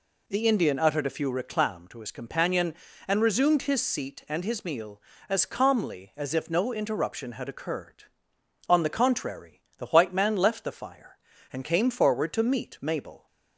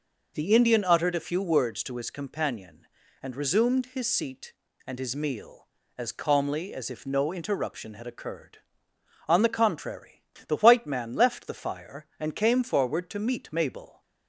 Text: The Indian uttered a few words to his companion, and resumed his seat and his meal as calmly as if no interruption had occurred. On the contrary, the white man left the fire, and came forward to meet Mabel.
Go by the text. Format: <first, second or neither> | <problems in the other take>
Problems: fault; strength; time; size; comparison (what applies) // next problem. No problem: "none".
second | says "reclam" for "words"; at 1.2 s